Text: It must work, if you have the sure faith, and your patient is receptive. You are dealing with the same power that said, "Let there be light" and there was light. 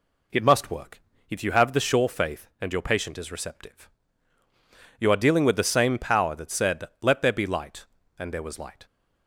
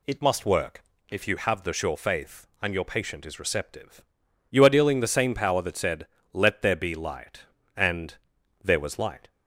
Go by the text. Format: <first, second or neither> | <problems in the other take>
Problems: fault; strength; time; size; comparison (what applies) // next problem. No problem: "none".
first | skips "with"; at 4.9 s // pauses between "and" and "there"; noticeable; at 8.1 s; 0.48 s long